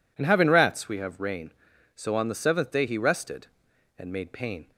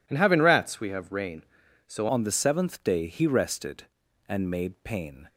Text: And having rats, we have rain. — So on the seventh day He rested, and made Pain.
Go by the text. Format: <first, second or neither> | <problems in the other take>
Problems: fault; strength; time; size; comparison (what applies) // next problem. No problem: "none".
first | changes voice at "on"; from 2.0 s on; 3.2 s long